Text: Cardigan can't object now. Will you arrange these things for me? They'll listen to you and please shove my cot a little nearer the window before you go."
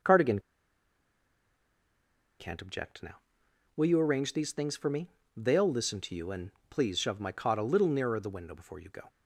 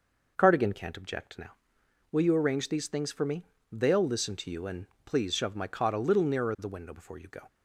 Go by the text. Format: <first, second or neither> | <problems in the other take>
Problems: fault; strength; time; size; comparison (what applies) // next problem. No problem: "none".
second | pauses between "Cardigan" and "can't"; strong; at 0.3 s; 2.0 s long // pauses between "and" and "please"; slight; at 6.5 s; 0.18 s long; slight in the second